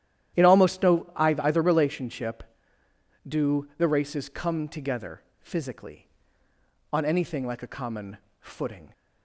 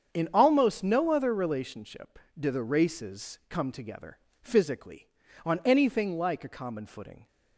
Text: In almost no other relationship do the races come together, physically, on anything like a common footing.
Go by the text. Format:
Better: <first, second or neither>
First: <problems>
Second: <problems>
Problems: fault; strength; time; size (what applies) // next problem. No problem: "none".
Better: second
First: starts louder than the rest; strong; until 1.4 s; 11.5 dB // says "either" for "other"; at 1.1 s // pauses between "common" and "footing"; slight; at 8.1 s; 0.22 s long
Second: starts louder than the rest; strong; until 1.1 s; 7.5 dB